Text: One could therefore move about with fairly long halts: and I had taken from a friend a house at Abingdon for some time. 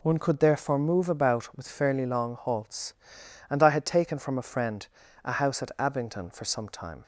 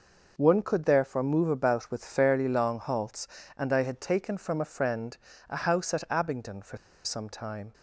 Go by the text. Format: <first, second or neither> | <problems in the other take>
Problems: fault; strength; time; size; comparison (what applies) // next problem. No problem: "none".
first | pauses between "friend" and "a"; slight; at 5.1 s; 0.32 s long; also in the first // pauses between "for" and "some"; slight; at 6.7 s; 0.27 s long